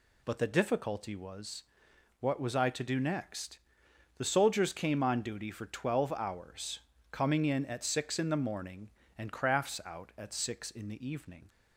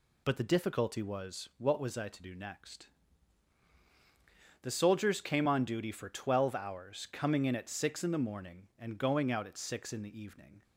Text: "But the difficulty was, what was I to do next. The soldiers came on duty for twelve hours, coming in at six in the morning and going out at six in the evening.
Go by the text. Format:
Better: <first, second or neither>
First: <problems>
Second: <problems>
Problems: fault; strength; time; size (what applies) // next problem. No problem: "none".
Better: second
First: says "crafts" for "going"; at 9.3 s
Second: none